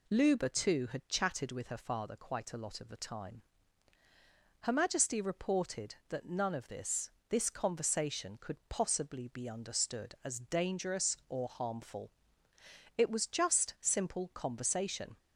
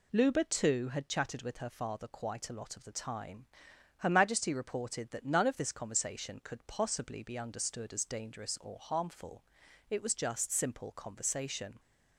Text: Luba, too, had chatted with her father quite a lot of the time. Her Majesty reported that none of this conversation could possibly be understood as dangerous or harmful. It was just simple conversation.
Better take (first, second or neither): second